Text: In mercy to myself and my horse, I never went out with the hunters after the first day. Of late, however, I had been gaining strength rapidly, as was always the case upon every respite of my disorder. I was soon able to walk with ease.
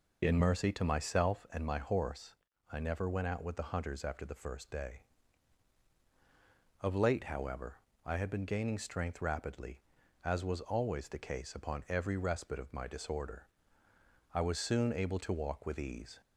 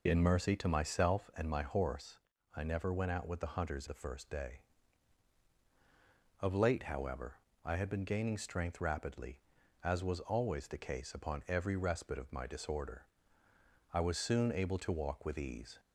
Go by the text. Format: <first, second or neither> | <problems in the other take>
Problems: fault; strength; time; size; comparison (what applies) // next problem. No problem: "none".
first | skips "after"; at 3.8 s